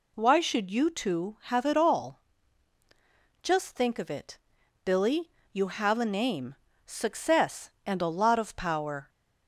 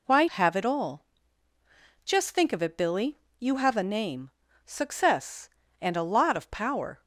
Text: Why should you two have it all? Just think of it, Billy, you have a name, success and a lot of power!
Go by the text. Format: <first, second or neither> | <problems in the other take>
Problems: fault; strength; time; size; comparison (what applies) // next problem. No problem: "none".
first | skips "should you two"; at 0.2 s